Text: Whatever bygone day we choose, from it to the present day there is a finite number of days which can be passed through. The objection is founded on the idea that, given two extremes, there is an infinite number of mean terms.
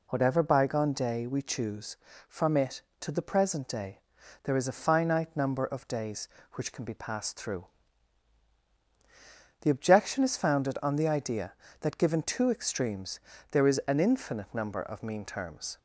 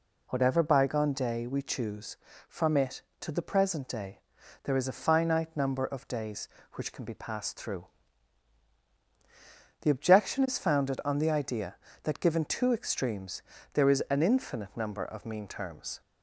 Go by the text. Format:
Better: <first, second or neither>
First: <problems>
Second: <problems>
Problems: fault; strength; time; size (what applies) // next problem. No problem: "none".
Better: neither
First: pauses between "day" and "there"; at 3.9 s; 0.44 s long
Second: pauses between "day" and "there"; at 4.1 s; 0.44 s long